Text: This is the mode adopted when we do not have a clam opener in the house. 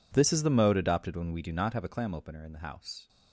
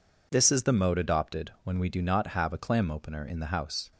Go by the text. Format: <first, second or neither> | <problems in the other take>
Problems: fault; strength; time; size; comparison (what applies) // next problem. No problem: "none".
second | gets quieter; strong; throughout; 23.5 dB